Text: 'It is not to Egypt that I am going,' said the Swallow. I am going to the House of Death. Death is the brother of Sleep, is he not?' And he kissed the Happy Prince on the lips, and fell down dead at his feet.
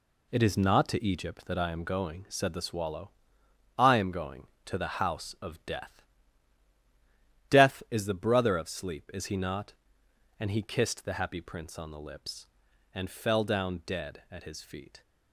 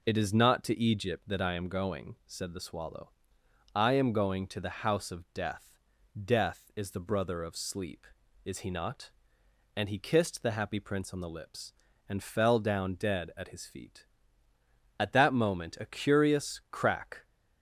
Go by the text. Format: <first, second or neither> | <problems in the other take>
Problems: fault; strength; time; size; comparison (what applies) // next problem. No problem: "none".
first | goes on to say "At that moment a curious crack"; strong; from 14.9 s on; 2.2 s long